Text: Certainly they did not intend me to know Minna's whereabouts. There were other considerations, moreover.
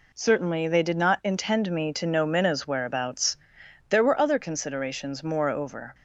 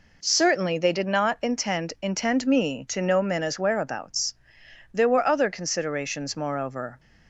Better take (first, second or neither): first